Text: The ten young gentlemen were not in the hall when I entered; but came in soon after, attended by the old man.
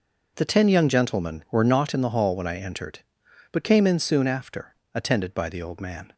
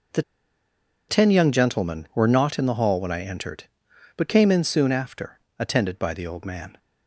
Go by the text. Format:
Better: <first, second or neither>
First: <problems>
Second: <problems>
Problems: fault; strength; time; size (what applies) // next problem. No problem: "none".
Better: first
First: none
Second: pauses between "The" and "ten"; noticeable; at 0.2 s; 0.87 s long